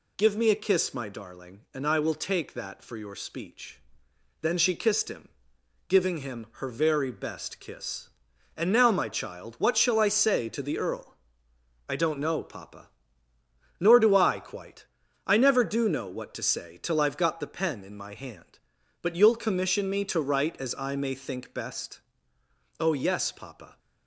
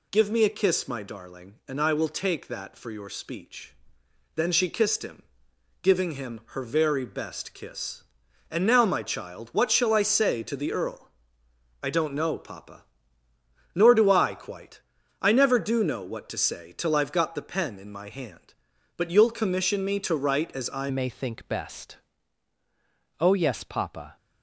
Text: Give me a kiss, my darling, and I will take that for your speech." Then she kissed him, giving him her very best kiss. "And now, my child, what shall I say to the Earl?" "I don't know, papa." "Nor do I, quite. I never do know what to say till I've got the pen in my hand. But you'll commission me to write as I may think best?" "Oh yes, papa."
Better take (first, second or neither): first